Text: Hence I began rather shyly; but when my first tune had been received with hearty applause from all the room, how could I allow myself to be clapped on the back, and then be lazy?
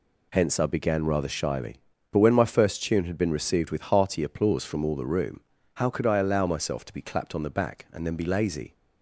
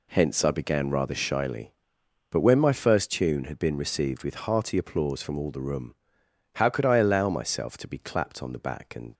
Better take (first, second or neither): first